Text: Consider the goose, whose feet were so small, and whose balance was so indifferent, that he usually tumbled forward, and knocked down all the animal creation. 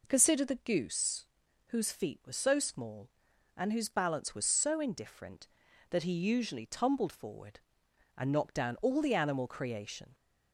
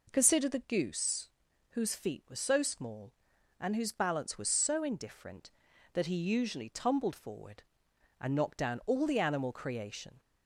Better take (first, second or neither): neither